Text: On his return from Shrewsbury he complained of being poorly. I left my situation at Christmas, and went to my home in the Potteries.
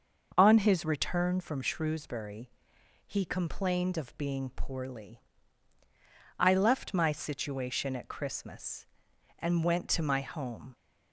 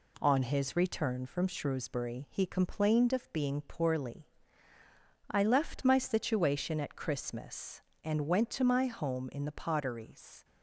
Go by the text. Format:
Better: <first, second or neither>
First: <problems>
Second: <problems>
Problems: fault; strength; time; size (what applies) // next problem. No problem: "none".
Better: second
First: starts louder than the rest; until 1.4 s; 6 dB // pauses between "Shrewsbury" and "he"; noticeable; at 2.4 s; 0.56 s long // stops before "in the Potteries"; at 10.7 s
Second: none